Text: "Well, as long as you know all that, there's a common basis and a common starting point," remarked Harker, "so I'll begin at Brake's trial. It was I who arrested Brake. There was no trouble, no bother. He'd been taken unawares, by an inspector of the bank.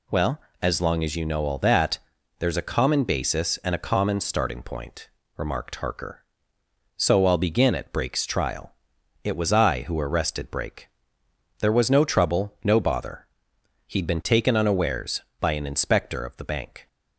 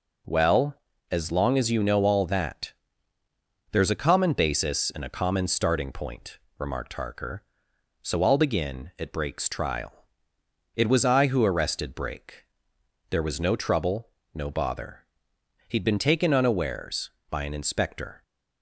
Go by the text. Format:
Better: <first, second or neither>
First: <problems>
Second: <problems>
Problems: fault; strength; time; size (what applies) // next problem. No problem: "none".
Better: first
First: none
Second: stops before "of the bank"; at 18.2 s